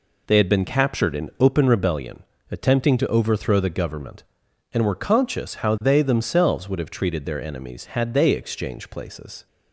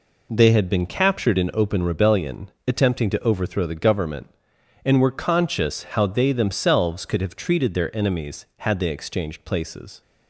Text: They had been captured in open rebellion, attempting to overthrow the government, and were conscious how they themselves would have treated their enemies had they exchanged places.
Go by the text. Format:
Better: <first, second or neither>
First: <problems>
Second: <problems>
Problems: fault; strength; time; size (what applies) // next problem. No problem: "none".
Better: first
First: none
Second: says "could" for "would"; at 7.0 s